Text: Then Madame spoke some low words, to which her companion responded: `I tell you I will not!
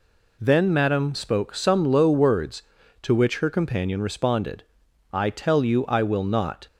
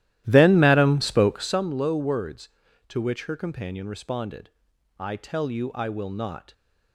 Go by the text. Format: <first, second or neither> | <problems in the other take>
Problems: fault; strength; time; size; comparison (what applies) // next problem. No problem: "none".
first | starts louder than the rest; strong; until 1.6 s; 14 dB